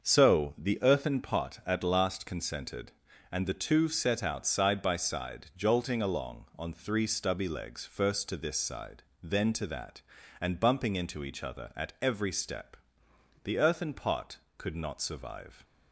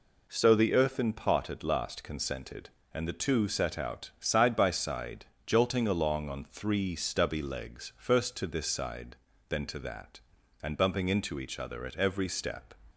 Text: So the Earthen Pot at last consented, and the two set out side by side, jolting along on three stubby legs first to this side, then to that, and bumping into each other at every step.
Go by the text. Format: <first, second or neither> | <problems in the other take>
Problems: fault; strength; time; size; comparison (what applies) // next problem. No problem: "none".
second | starts louder than the rest; until 1.0 s; 6.5 dB // goes on to say "The Earthen Pot could not survive"; strong; from 13.4 s on; 2.2 s long